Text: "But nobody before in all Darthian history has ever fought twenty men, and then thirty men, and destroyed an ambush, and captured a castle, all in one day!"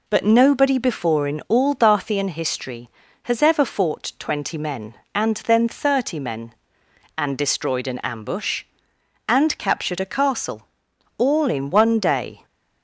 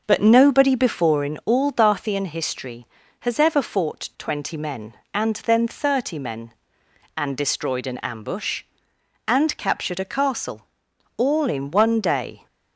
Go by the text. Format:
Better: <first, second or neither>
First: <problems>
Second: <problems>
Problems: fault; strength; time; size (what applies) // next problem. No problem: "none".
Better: first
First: none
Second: starts louder than the rest; noticeable; until 1.3 s; 6 dB